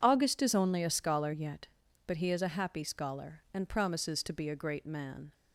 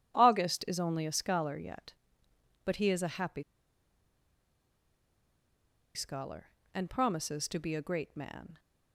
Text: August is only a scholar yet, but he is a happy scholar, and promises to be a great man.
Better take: first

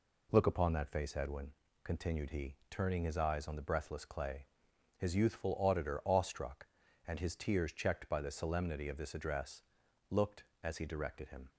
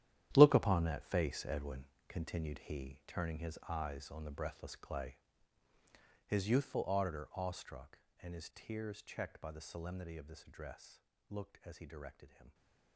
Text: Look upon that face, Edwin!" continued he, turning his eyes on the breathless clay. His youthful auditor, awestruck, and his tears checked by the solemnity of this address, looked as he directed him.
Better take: first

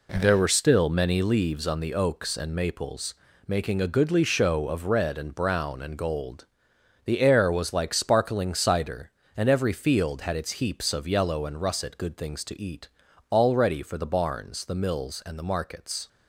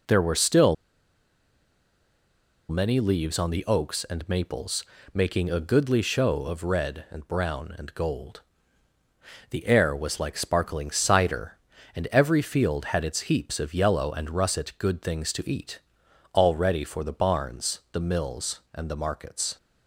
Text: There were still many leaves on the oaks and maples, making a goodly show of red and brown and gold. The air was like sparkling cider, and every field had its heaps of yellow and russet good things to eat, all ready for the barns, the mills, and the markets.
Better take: first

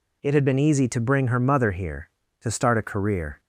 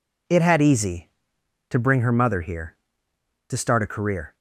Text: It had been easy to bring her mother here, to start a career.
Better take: first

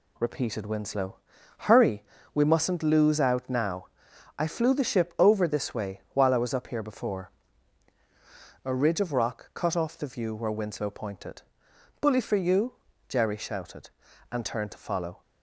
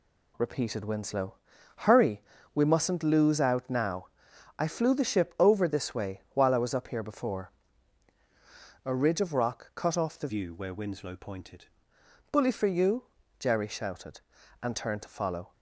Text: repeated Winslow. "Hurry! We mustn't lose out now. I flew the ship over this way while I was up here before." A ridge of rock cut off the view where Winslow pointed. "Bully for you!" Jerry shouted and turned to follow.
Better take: first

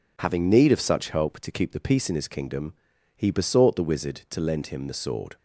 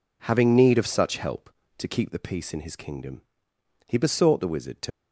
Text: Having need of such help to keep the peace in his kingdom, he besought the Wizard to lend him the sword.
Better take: first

